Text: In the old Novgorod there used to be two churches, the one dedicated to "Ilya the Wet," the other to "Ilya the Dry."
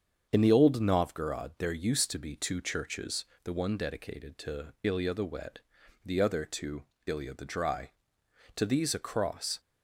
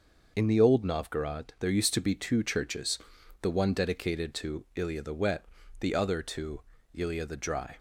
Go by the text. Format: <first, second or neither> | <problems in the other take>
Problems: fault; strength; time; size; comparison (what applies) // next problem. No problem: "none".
second | starts louder than the rest; until 1.3 s; 7 dB // pauses between "to" and "Ilya"; slight; at 6.8 s; 0.22 s long; slight in the second // goes on to say "To these a cross"; noticeable; from 8.5 s on; 1.0 s long